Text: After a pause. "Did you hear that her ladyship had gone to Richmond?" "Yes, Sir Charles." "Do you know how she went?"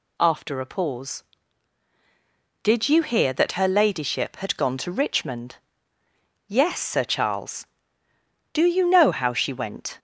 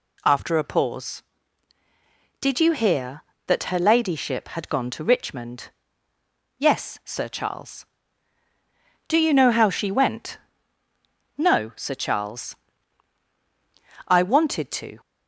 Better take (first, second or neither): first